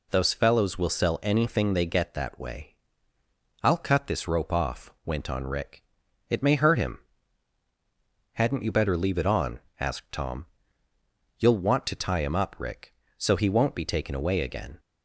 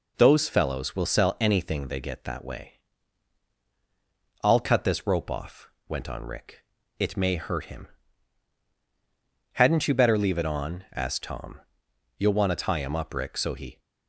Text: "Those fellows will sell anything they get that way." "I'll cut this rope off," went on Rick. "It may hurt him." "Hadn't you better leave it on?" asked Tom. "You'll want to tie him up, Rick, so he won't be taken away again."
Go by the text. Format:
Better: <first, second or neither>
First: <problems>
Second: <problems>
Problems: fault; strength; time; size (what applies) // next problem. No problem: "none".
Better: first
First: none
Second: stops before "won't be taken away again"; at 13.7 s